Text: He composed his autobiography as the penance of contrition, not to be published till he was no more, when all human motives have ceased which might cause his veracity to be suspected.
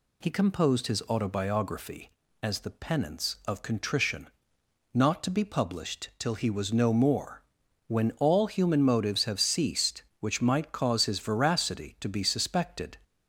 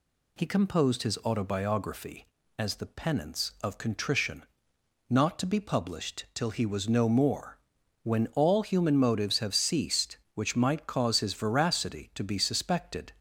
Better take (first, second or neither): neither